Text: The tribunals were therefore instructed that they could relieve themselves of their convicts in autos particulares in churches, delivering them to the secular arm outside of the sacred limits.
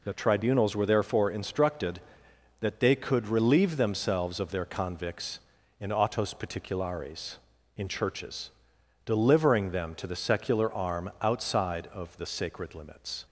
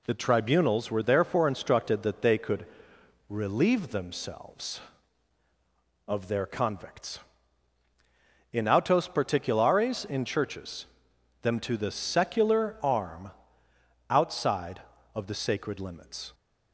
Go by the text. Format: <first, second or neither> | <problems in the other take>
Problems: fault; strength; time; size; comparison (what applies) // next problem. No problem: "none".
first | pauses between "could" and "relieve"; noticeable; at 2.6 s; 0.64 s long // skips "delivering"; at 11.1 s // pauses between "arm" and "outside"; noticeable; at 13.3 s; 0.78 s long